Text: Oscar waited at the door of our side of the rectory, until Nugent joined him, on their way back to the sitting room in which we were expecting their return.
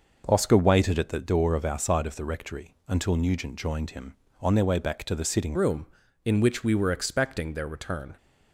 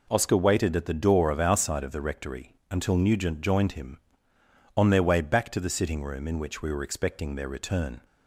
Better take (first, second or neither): second